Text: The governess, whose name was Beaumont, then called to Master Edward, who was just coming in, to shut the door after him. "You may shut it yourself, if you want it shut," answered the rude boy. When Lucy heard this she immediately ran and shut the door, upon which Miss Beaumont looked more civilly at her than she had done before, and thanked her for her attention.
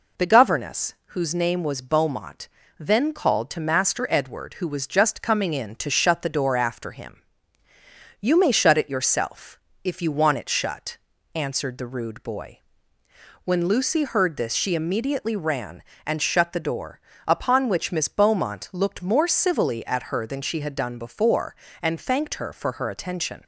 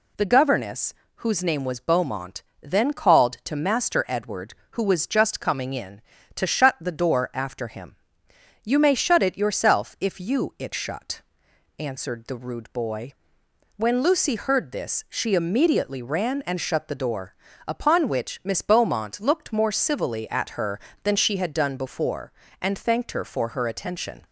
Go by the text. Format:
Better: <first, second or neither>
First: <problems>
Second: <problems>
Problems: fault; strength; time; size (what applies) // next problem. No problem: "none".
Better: first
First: none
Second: skips "want"; at 10.5 s